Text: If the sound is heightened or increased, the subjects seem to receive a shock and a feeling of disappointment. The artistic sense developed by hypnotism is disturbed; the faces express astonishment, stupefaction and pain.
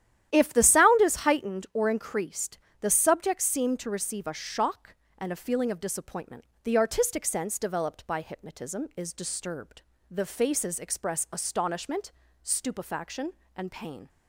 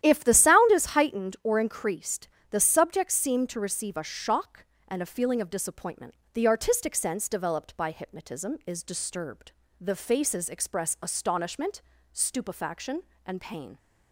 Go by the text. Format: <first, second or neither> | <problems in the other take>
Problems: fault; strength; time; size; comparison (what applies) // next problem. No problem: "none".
neither | starts louder than the rest; strong; the same in both